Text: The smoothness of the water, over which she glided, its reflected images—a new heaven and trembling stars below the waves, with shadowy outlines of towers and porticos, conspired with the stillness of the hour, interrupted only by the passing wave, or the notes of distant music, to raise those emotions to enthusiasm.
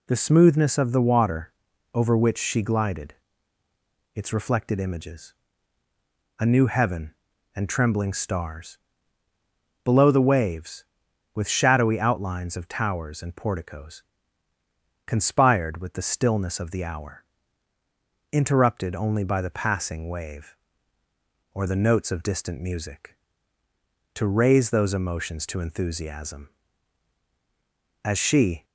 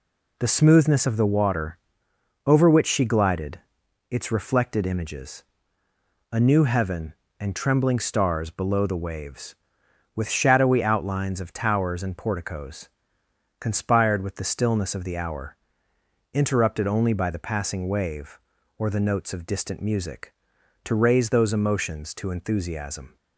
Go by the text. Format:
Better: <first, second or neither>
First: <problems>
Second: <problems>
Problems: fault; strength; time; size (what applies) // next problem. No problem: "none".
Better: second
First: pauses between "stars" and "below"; at 8.7 s; 1.0 s long // goes on to say "As she"; noticeable; from 28.0 s on; 0.62 s long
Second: none